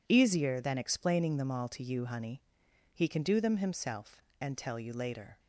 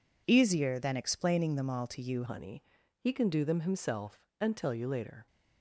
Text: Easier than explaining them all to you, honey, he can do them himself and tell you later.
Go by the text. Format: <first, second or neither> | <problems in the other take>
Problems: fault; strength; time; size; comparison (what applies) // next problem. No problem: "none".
first | changes voice at "honey"; from 2.2 s on; 3.0 s long